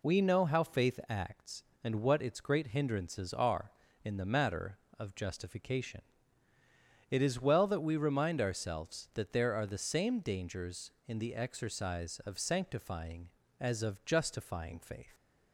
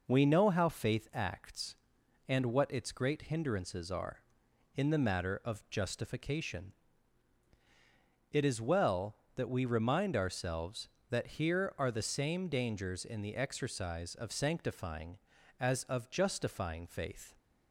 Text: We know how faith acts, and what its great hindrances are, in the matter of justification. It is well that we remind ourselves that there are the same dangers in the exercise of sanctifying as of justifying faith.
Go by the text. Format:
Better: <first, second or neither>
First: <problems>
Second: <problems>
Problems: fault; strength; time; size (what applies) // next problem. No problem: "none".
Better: first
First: none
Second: says "here" for "there"; at 11.2 s